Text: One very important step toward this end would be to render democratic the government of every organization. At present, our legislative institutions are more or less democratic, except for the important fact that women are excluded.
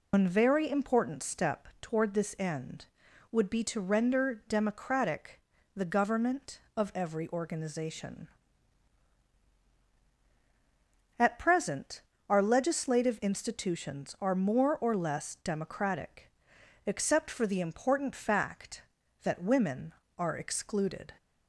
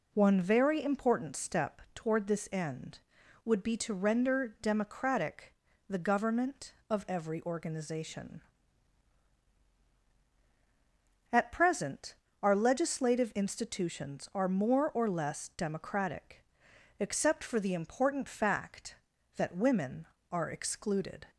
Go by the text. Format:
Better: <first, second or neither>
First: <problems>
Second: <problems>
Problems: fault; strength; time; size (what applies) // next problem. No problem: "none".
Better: second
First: loses the start of "One"; at 0.1 s; 135 ms // pauses between "democratic" and "the"; slight; at 5.3 s; 0.36 s long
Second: pauses between "democratic" and "the"; slight; at 5.5 s; 0.36 s long